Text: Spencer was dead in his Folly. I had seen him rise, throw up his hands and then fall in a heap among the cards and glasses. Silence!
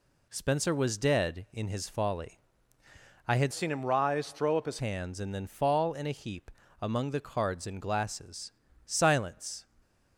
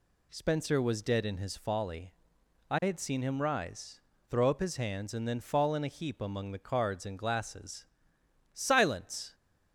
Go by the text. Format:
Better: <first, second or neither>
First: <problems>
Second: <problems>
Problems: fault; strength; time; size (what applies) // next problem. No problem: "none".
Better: second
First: changes voice from "seen" to "his"; from 3.5 to 4.7 s; 1.2 s long // pauses between "heap" and "among"; slight; at 6.4 s; 0.32 s long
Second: none